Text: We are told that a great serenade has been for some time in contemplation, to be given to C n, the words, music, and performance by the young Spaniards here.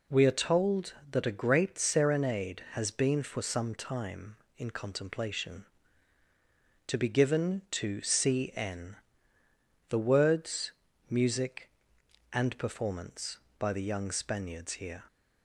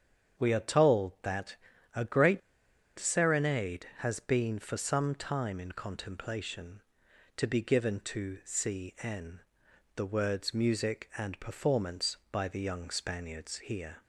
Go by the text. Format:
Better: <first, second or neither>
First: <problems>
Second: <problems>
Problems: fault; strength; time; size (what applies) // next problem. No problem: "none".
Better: first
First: none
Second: starts louder than the rest; strong; until 1.4 s; 7.5 dB // pauses between "that" and "a"; at 1.5 s; 0.40 s long // pauses between "great" and "serenade"; noticeable; at 2.4 s; 0.58 s long